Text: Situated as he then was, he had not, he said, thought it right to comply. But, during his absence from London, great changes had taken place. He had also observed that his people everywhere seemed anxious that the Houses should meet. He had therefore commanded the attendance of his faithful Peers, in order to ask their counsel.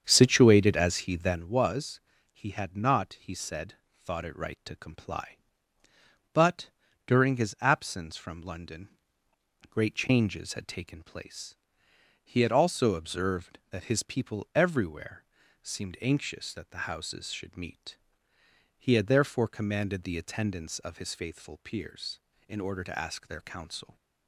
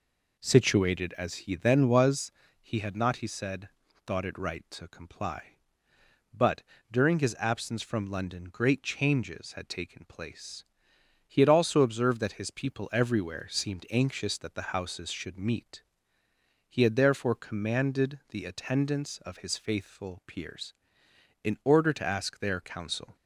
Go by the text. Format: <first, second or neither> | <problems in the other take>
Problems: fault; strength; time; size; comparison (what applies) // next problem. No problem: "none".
second | starts louder than the rest; strong; until 1.5 s; 8 dB // pauses between "everywhere" and "seemed"; at 15.2 s; 0.40 s long